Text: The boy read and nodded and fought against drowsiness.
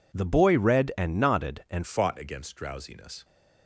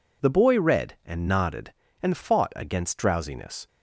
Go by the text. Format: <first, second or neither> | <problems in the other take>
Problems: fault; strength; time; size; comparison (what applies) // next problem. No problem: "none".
second | changes voice at "fought"; from 1.8 s on; 1.4 s long